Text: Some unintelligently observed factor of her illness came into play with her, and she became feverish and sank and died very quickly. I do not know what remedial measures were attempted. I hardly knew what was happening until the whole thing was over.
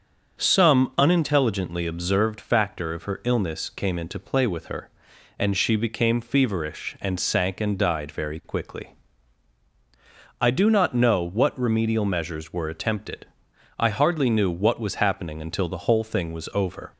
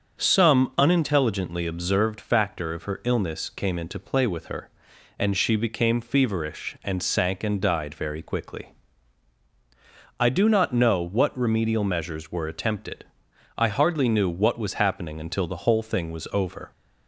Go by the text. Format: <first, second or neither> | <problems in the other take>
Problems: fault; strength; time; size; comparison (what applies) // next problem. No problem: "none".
neither | starts louder than the rest; the same in both